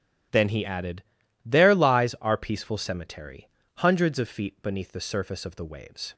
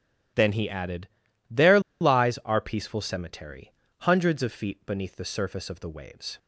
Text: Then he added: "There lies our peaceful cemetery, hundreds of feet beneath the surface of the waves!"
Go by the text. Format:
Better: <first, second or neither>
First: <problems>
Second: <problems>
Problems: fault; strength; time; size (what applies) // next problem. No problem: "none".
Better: first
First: starts louder than the rest; strong; until 1.7 s; 12 dB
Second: starts louder than the rest; strong; until 1.7 s; 12.5 dB // pauses between "There" and "lies"; slight; at 1.7 s; 0.21 s long